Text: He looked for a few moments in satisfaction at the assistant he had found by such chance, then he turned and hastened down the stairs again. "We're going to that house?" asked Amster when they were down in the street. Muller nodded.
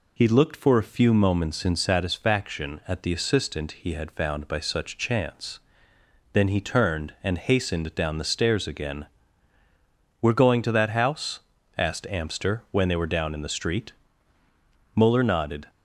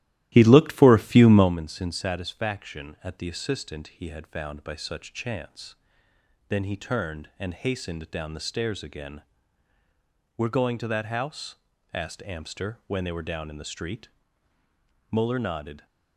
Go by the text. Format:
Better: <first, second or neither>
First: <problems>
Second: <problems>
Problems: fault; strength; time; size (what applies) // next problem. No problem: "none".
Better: first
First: none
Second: starts louder than the rest; strong; until 1.6 s; 15 dB